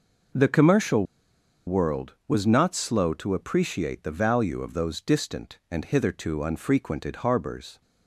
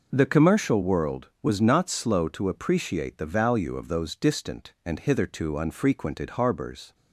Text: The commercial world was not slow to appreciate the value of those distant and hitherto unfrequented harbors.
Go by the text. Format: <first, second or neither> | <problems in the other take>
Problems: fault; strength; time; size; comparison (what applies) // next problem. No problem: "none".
second | pauses between "commercial" and "world"; noticeable; at 1.0 s; 0.61 s long